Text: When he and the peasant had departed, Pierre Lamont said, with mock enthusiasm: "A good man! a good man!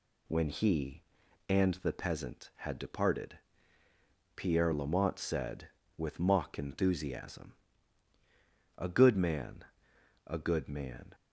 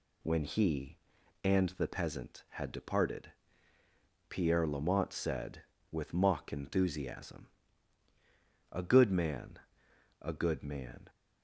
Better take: neither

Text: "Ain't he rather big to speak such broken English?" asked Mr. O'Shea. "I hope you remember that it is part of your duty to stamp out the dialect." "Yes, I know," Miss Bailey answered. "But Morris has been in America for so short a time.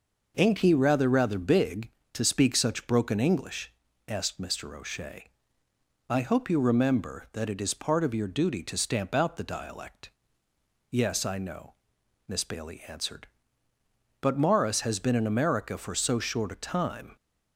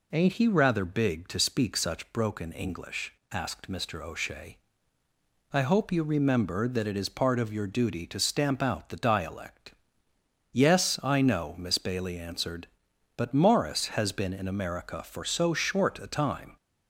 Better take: second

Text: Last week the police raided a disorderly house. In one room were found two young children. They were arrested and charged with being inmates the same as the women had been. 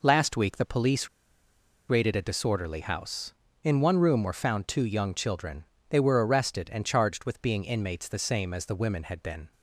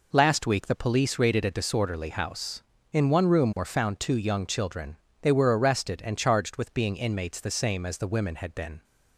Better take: second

